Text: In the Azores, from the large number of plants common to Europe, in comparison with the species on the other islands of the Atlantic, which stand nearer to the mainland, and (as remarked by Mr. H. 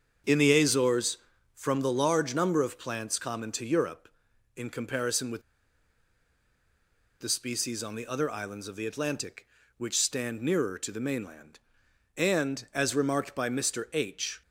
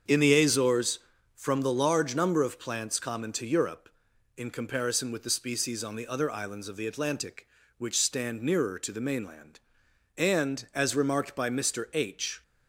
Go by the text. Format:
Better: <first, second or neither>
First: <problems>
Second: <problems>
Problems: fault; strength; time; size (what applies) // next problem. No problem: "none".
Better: second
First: starts louder than the rest; strong; until 1.5 s; 7 dB // pauses between "with" and "the"; strong; at 5.4 s; 1.7 s long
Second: starts louder than the rest; strong; until 1.4 s; 7 dB